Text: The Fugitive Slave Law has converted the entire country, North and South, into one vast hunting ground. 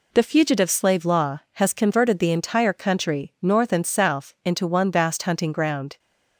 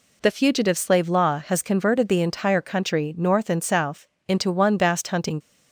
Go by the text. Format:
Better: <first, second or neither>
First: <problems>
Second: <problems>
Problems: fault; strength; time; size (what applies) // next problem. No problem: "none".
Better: first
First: none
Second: stops before "ground"; at 5.4 s